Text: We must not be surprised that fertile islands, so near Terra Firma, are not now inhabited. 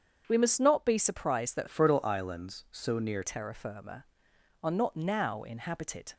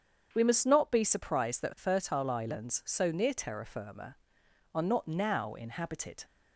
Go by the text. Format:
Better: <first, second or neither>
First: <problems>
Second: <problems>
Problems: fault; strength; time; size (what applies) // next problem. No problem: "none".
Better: second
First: starts louder than the rest; strong; until 1.2 s; 7.5 dB // changes voice from "fertile" to "near"; from 1.6 to 3.2 s; 1.6 s long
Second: starts louder than the rest; strong; until 1.3 s; 7.5 dB